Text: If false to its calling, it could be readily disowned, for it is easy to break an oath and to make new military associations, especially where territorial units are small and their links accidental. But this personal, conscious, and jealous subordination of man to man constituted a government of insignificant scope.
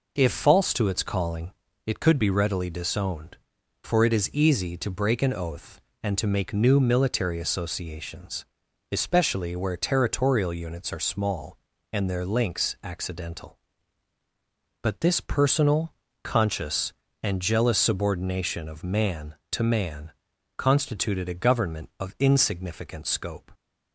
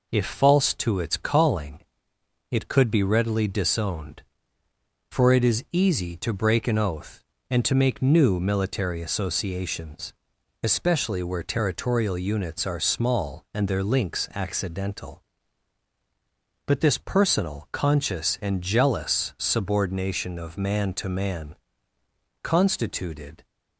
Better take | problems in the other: first | pauses between "man" and "constituted"; noticeable; at 21.5 s; 0.88 s long; also in the first // stops before "a government of insignificant scope"; at 23.4 s

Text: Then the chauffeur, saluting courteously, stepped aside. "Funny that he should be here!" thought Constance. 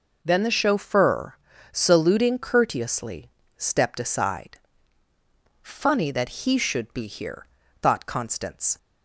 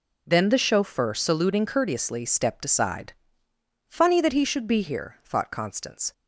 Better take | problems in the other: neither | none

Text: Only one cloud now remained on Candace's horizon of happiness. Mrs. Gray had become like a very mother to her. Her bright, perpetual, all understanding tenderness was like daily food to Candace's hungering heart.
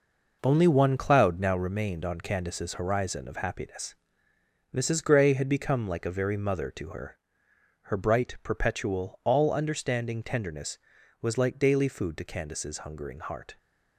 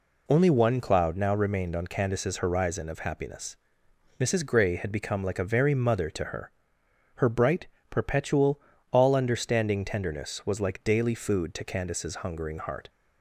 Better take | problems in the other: second | gets quieter; strong; throughout; 7.5 dB

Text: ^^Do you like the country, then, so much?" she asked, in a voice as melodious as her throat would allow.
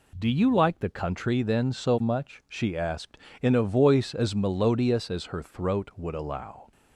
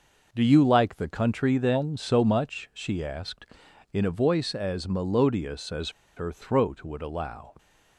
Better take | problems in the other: first | pauses between "as" and "her"; slight; at 5.8 s; 0.27 s long

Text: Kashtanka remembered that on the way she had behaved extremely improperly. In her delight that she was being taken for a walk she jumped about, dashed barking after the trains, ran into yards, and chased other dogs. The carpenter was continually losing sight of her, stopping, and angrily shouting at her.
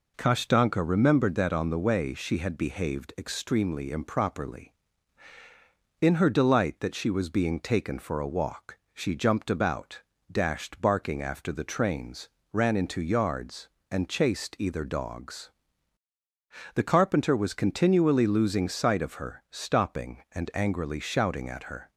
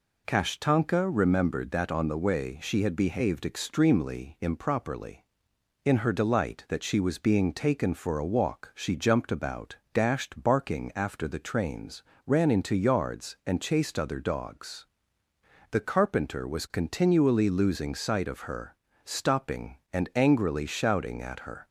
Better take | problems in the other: second | pauses between "walk" and "she"; slight; at 8.7 s; 0.18 s long // says "either" for "other"; at 14.5 s

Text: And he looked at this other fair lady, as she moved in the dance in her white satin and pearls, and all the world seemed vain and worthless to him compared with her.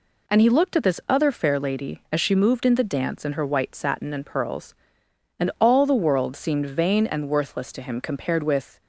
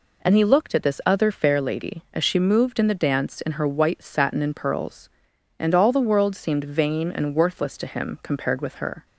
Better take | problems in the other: second | stops before "her"; at 8.8 s

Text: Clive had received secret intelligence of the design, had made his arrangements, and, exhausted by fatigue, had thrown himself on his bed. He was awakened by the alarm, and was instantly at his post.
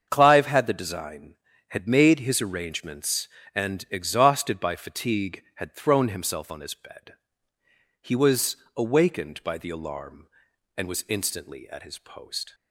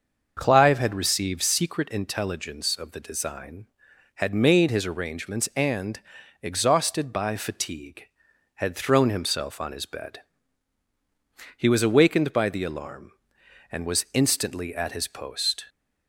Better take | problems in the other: second | starts louder than the rest; until 1.1 s; 7 dB; also in the second // skips "received secret intelligence of"; at 0.6 s // pauses between "was" and "awakened"; slight; at 8.5 s; 0.20 s long

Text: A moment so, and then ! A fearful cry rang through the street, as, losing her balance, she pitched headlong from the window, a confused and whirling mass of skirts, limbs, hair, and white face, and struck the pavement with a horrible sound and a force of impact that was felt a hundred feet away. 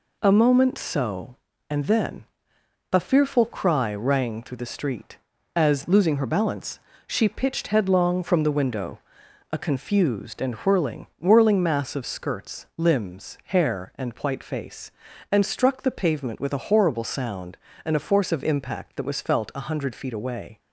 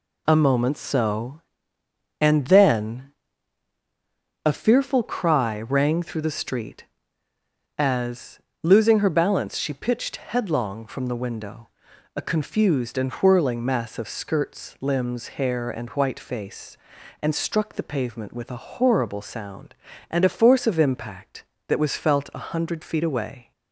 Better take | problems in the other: second | says "whirling" twice; at 11.2 s

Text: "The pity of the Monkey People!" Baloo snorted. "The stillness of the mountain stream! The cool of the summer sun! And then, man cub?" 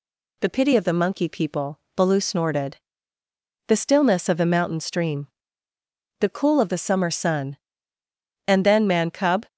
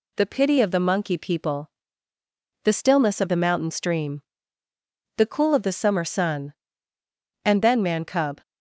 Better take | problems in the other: first | skips "Baloo snorted"; at 2.1 s

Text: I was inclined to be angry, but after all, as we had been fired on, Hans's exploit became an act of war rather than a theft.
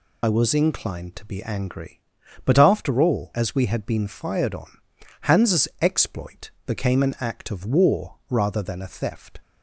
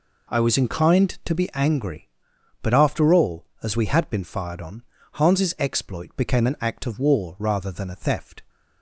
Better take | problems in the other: second | loses the start of "I"; at 0.2 s; 40 ms // pauses between "exploit" and "became"; slight; at 6.4 s; 0.16 s long

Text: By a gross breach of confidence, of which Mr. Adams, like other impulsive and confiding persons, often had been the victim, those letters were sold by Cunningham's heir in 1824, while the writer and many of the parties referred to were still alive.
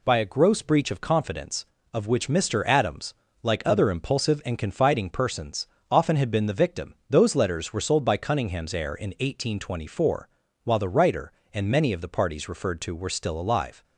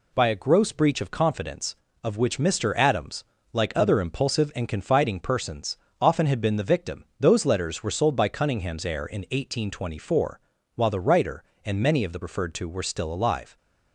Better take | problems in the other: first | skips "parties"; at 12.2 s

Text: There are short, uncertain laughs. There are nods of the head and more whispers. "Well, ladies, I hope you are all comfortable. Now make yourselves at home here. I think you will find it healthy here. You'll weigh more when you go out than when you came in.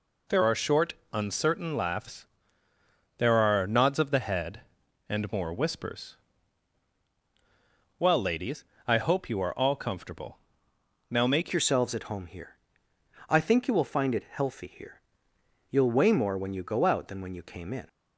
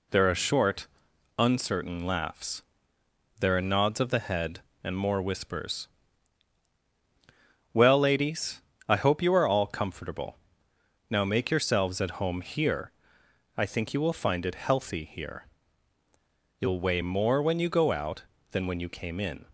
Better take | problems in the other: second | changes voice at "yourselves"; from 11.5 s on; 6.3 s long

